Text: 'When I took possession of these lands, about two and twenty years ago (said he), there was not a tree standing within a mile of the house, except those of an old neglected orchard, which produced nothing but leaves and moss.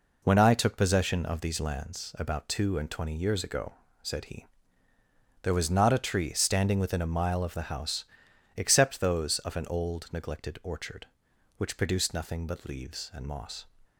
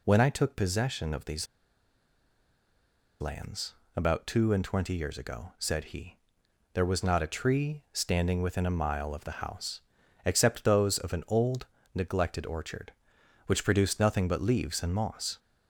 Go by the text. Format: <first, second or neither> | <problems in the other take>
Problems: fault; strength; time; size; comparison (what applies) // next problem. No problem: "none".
first | pauses between "these" and "lands"; strong; at 1.4 s; 1.7 s long // pauses between "old" and "neglected"; slight; at 11.6 s; 0.28 s long